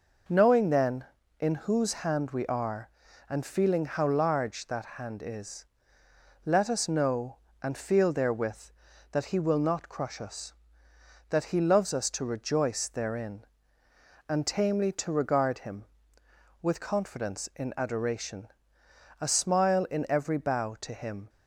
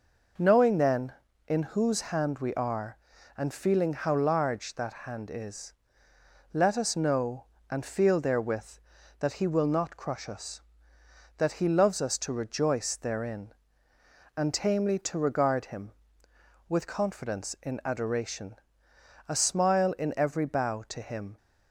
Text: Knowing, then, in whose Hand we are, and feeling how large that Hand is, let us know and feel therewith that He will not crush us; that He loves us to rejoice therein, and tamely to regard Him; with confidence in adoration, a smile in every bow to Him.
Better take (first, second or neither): neither